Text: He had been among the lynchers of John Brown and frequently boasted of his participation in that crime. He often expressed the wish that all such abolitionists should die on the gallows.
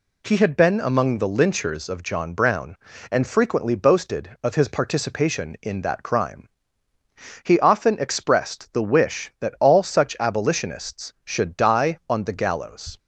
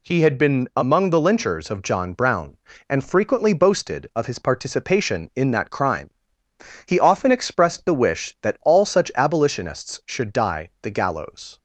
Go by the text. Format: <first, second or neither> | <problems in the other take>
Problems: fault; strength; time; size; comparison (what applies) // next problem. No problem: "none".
first | skips "on"; at 10.7 s